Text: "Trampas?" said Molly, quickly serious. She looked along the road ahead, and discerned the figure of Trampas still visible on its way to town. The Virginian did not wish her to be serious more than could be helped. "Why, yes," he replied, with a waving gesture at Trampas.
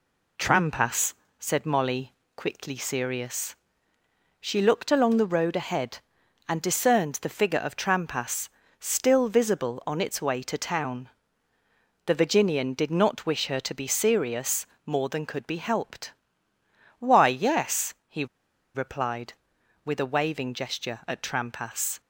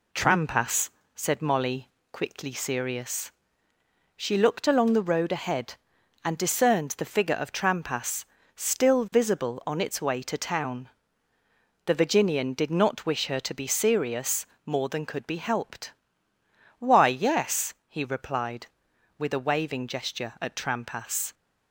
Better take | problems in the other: second | pauses between "Trampas" and "still"; slight; at 8.4 s; 0.28 s long; slight in the second // pauses between "serious" and "more"; slight; at 14.6 s; 0.18 s long; slight in the second // pauses between "he" and "replied"; noticeable; at 18.2 s; 0.48 s long

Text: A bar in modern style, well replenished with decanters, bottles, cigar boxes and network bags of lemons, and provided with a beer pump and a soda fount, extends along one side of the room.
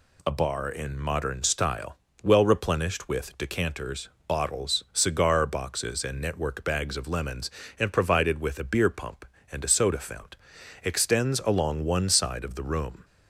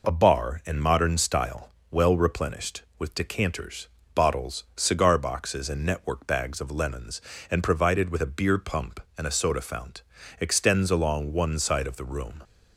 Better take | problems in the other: neither | none

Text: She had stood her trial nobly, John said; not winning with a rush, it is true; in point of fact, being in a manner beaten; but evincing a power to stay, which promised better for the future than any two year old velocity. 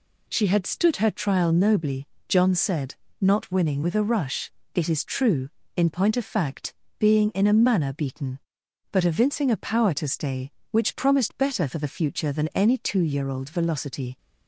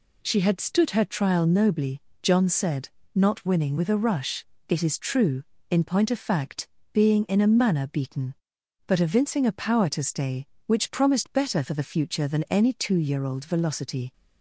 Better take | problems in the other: neither | none

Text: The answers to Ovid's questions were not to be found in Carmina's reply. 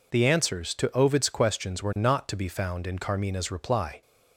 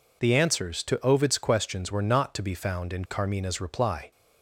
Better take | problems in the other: neither | none

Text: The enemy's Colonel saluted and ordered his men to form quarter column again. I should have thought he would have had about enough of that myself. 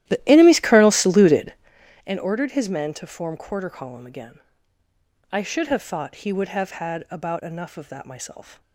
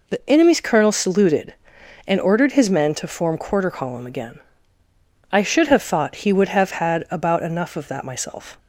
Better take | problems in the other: second | starts louder than the rest; strong; until 1.8 s; 13.5 dB

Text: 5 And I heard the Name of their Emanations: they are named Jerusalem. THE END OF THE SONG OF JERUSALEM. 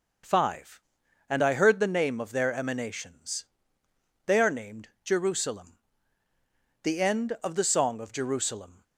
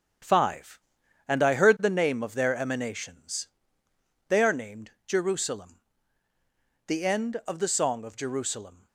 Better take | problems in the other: first | gets quieter; strong; throughout; 7.5 dB // pauses between "named" and "Jerusalem"; slight; at 4.8 s; 0.16 s long; slight in the first

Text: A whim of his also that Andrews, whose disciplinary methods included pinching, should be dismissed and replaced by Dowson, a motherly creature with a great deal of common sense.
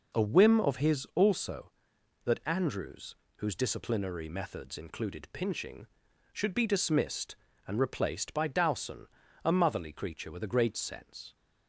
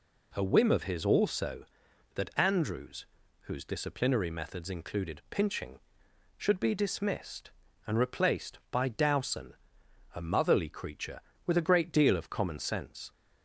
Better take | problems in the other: second | skips "deal of common"; at 10.7 s

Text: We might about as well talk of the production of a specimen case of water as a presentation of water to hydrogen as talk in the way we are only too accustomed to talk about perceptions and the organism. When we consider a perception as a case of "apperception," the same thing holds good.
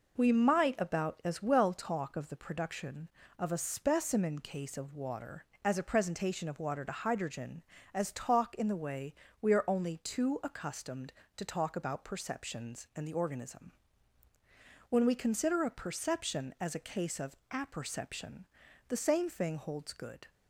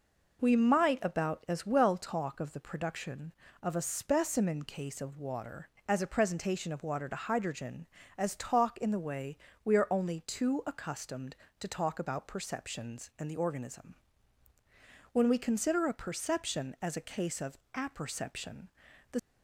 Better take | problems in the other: first | pauses between "way" and "we"; slight; at 9.3 s; 0.30 s long; slight in the first // pauses between "of" and "apperception"; slight; at 17.5 s; 0.16 s long // stops before "same thing holds good"; at 19.1 s

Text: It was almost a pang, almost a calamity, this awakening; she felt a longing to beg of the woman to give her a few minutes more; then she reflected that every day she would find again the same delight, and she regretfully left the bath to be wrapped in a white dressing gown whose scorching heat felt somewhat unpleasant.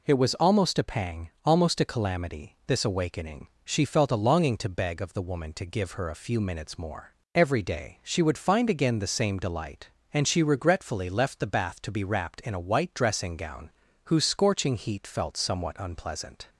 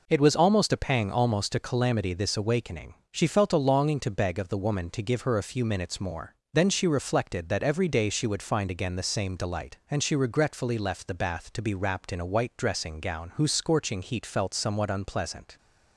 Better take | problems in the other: second | skips "then she reflected that"; at 7.2 s // pauses between "gown" and "whose"; slight; at 13.7 s; 0.36 s long

